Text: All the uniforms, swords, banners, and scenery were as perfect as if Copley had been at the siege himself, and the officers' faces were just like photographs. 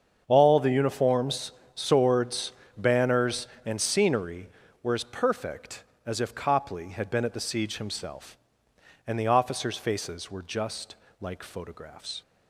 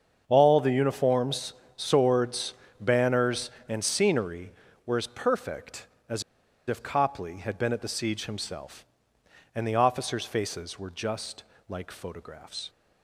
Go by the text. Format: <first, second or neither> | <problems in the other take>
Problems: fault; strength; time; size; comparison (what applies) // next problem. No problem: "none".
first | starts louder than the rest; strong; until 1.2 s; 7 dB; strong in the first // pauses between "as" and "if"; at 6.2 s; 0.44 s long // pauses between "just" and "like"; slight; at 11.4 s; 0.26 s long; slight in the first